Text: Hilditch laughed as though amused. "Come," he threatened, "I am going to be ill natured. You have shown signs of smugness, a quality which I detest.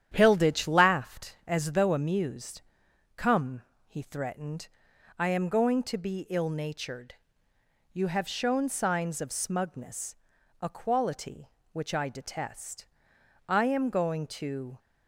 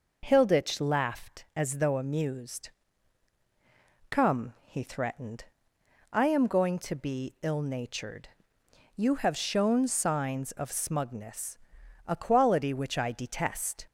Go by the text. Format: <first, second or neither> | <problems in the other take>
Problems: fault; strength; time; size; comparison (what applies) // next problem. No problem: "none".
second | starts louder than the rest; strong; until 1.1 s; 10 dB // goes on to say "I am going to"; from 13.4 s on; 1.3 s long